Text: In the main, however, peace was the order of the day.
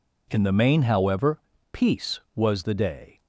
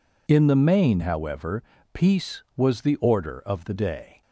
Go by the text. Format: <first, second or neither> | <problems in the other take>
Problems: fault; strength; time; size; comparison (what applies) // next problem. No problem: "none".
second | skips "the order of"; at 2.6 s